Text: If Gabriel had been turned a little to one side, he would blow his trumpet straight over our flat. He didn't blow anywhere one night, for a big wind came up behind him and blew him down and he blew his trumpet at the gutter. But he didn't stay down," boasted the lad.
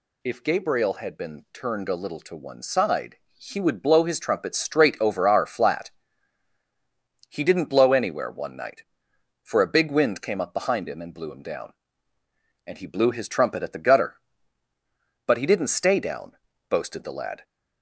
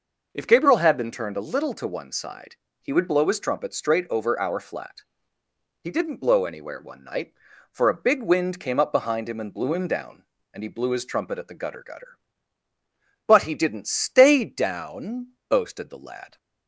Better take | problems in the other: first | says "gutter" twice; at 11.8 s

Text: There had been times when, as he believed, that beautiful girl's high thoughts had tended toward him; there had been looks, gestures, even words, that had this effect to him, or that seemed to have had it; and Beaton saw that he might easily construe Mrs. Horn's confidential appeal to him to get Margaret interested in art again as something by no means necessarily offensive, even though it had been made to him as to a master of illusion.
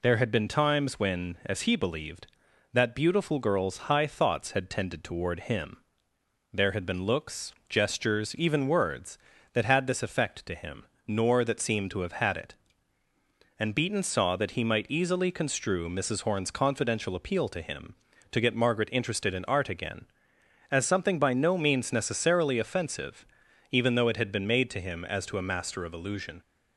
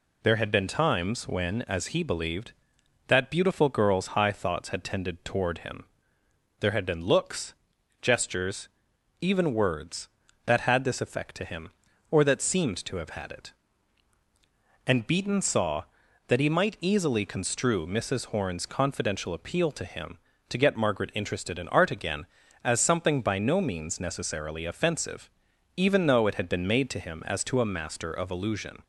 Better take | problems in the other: second | says "nor" for "or"; at 11.0 s

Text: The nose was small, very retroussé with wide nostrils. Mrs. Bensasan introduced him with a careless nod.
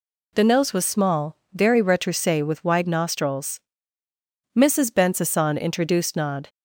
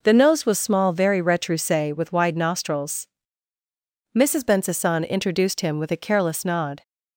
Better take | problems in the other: second | skips "him with a careless"; at 6.1 s

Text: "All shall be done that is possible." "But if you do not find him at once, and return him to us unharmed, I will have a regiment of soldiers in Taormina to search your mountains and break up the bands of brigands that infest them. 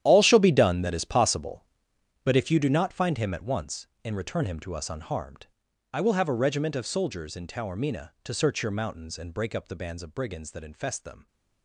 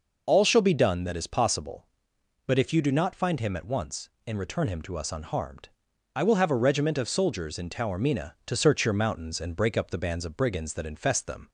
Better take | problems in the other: second | gets quieter; strong; throughout; 14.5 dB

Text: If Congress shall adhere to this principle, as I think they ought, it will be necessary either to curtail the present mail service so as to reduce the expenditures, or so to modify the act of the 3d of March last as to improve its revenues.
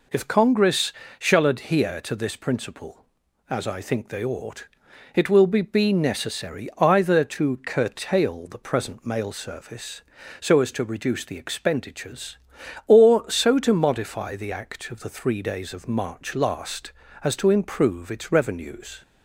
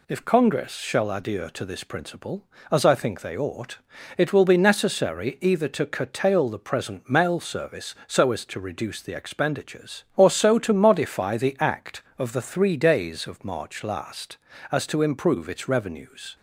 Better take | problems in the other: second | pauses between "Congress" and "shall"; slight; at 0.9 s; 0.28 s long // says "be" twice; at 5.6 s

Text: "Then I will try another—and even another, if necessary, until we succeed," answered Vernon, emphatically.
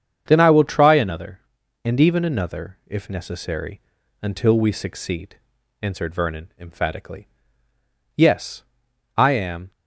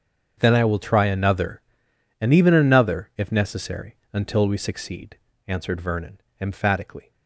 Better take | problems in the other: second | starts louder than the rest; strong; until 1.2 s; 7.5 dB; also in the second // goes on to say "Yes I am"; from 8.1 s on; 1.5 s long

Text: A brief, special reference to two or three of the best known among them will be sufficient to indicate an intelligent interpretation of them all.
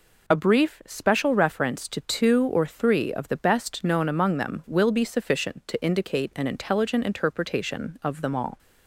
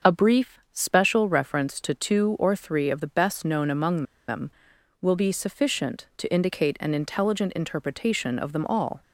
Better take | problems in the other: first | starts louder than the rest; until 1.1 s; 6.5 dB // pauses between "among" and "them"; slight; at 4.0 s; 0.25 s long

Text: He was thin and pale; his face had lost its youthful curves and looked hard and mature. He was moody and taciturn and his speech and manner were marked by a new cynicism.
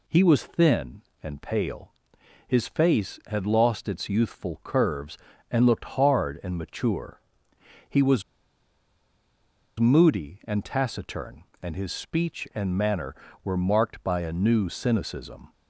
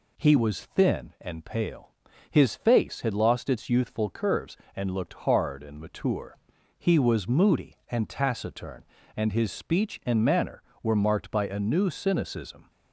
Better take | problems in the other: second | pauses between "was" and "moody"; strong; at 8.2 s; 1.5 s long

